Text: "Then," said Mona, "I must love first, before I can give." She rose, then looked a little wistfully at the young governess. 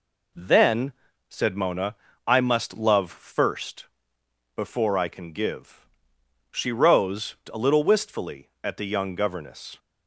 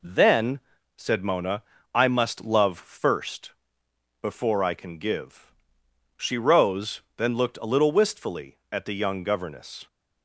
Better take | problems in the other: second | skips "then looked"; at 7.4 s

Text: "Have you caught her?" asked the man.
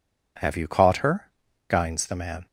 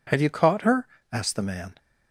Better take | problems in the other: second | says "guines" for "asked"; at 1.6 s

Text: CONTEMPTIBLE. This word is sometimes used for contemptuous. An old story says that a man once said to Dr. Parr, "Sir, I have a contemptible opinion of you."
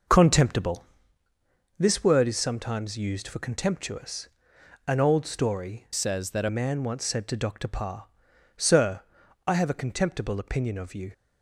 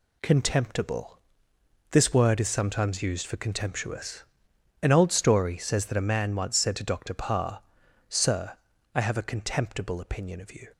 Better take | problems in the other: second | changes voice from "says" to "a"; from 5.9 to 6.4 s; 0.5 s long

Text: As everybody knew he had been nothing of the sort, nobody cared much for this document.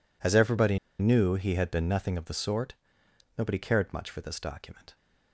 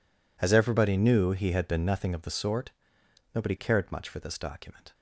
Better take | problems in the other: second | pauses between "everybody" and "knew"; slight; at 0.7 s; 0.21 s long

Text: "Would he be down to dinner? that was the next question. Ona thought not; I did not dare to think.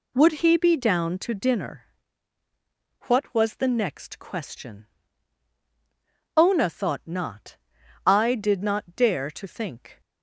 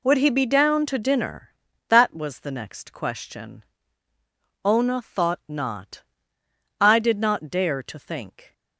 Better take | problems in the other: second | says "what" for "that"; at 3.0 s

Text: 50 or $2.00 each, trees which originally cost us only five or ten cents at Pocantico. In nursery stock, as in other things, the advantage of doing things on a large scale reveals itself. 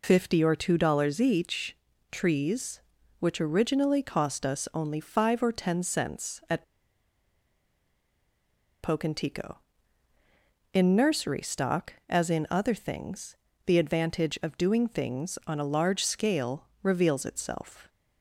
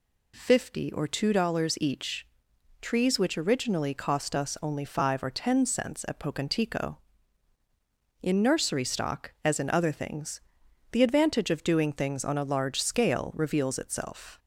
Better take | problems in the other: second | pauses between "at" and "Pocantico"; strong; at 6.6 s; 2.2 s long

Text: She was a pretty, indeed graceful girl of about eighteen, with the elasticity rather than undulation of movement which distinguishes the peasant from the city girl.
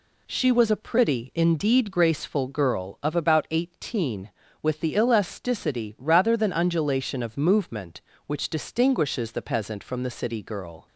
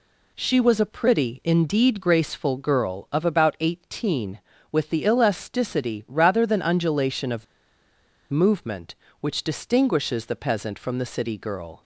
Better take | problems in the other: first | pauses between "of" and "movement"; noticeable; at 7.4 s; 0.84 s long

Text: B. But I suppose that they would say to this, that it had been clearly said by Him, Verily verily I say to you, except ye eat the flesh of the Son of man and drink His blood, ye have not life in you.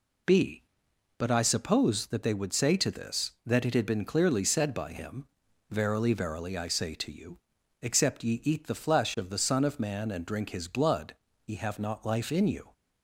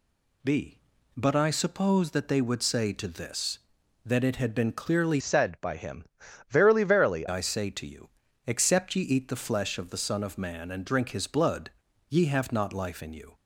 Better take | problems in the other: first | changes voice from "said" to "verily"; from 5.1 to 7.2 s; 2.1 s long

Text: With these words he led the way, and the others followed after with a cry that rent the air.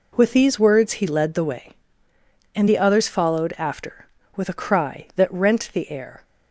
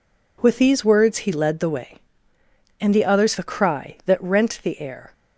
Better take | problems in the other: first | skips "followed after with"; at 3.3 s

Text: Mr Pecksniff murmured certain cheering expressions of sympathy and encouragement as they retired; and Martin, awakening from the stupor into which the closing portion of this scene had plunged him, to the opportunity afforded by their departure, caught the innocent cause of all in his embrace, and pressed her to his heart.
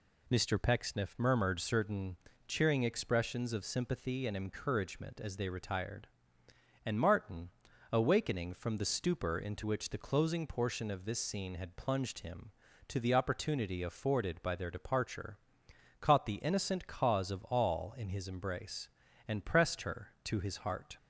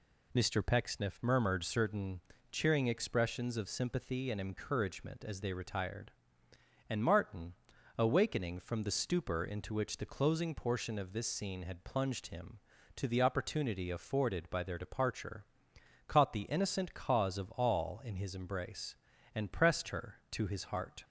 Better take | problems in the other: neither | pauses between "certain" and "cheering"; slight; the same in both

